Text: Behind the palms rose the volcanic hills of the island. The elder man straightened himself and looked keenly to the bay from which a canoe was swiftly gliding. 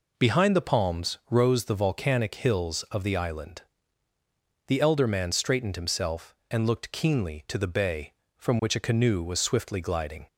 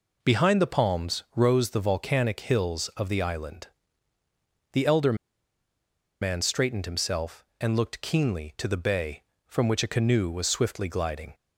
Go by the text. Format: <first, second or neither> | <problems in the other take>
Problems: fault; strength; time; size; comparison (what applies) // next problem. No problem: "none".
first | pauses between "elder" and "man"; at 5.1 s; 1.0 s long